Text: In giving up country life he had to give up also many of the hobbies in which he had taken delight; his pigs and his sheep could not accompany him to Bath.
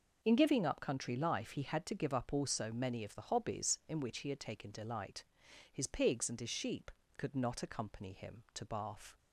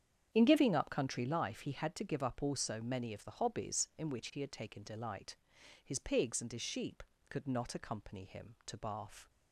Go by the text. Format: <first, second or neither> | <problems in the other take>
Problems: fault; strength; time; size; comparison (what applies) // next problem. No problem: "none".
first | starts louder than the rest; strong; until 1.4 s; 8.5 dB